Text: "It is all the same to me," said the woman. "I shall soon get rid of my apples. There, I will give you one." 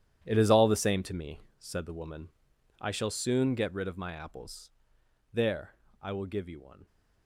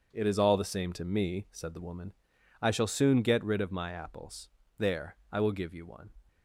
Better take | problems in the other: second | gets quieter; strong; throughout; 13 dB // starts louder than the rest; strong; until 1.2 s; 10.5 dB; also in the second

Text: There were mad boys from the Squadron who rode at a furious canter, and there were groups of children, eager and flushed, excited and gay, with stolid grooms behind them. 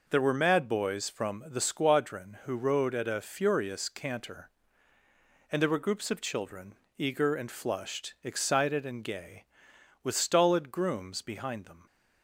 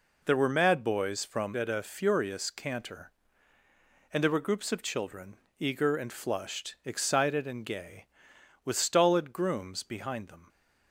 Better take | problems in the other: first | skips "the Squadron who rode"; at 1.5 s

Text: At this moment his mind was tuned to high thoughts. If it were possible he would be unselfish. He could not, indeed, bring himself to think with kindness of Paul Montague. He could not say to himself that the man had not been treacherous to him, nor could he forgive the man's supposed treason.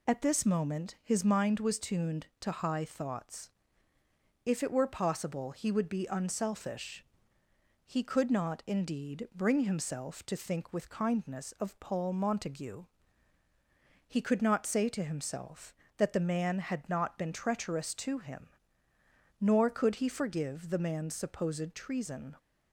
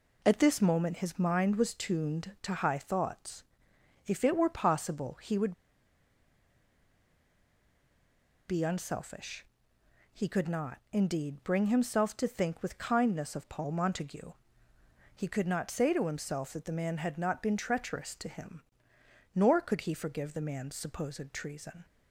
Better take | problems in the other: first | pauses between "would" and "be"; strong; at 5.5 s; 2.9 s long

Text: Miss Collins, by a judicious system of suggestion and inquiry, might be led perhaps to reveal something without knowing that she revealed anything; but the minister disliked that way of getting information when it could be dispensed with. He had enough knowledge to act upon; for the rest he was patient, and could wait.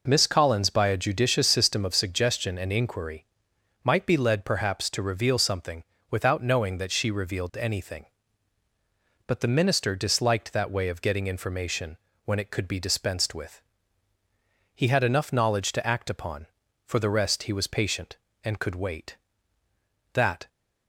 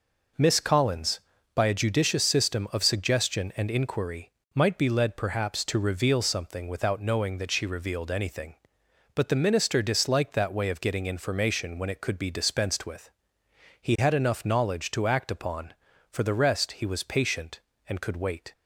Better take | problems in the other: second | pauses between "something" and "without"; slight; at 5.8 s; 0.28 s long // pauses between "information" and "when"; slight; at 11.9 s; 0.30 s long // goes on to say "That"; slight; from 20.1 s on; 0.34 s long

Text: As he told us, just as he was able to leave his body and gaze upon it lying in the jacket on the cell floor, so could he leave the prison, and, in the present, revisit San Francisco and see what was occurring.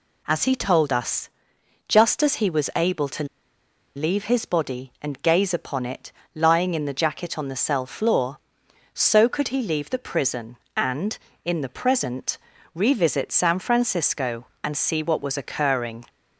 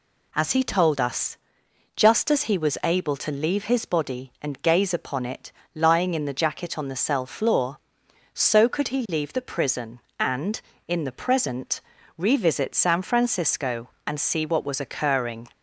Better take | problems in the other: second | pauses between "to" and "leave"; noticeable; at 3.2 s; 0.70 s long // pauses between "it" and "lying"; slight; at 6.1 s; 0.24 s long; slight in the second

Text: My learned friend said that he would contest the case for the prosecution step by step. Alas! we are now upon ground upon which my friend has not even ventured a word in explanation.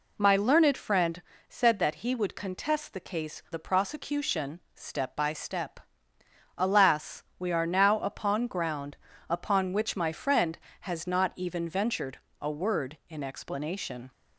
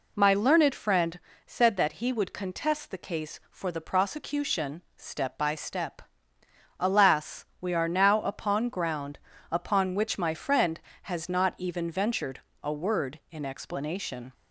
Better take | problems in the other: second | pauses between "friend" and "said"; slight; at 1.2 s; 0.28 s long; slight in the second // skips "for"; at 3.4 s // pauses between "prosecution" and "step"; slight; at 4.5 s; 0.16 s long; slight in the second // pauses between "ground" and "upon"; slight; at 8.9 s; 0.34 s long; slight in the second // pauses between "ventured" and "a"; slight; at 12.1 s; 0.20 s long; slight in the second

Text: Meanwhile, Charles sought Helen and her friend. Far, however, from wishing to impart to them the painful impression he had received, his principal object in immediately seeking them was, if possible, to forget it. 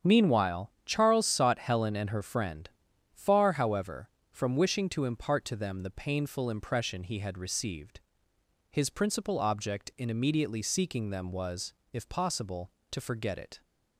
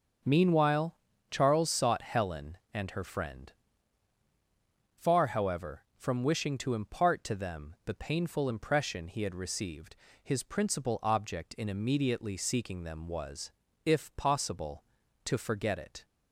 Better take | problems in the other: neither | starts louder than the rest; the same in both

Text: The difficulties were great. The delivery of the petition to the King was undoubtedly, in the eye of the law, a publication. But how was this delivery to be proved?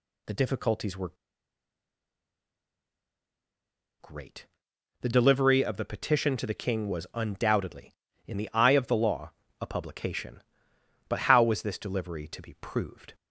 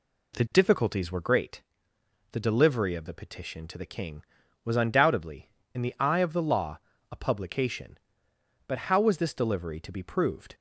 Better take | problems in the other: second | pauses between "were" and "great"; strong; at 1.1 s; 2.8 s long

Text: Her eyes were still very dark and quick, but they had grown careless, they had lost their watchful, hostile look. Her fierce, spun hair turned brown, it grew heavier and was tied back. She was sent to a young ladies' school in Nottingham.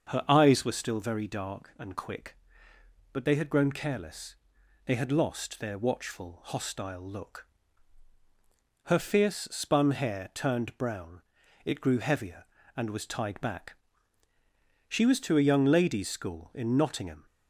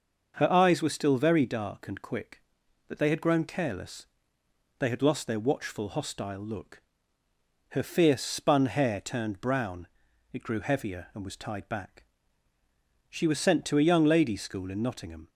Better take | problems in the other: second | starts louder than the rest; until 1.1 s; 6.5 dB; noticeable in the second // skips "sent"; at 15.1 s

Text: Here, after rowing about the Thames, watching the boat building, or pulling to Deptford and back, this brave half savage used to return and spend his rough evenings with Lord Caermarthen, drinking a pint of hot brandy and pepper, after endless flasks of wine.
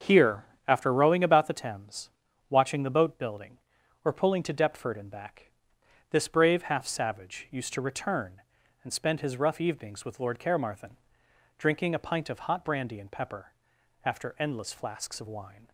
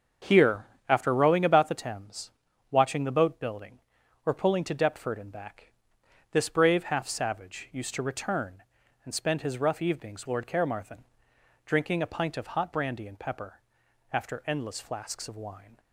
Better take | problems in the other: first | starts louder than the rest; until 1.4 s; 6.5 dB; also in the first // skips "with"; at 10.2 s

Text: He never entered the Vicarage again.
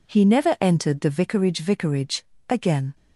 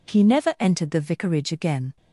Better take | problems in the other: second | says "Vicarage" twice; at 1.5 s

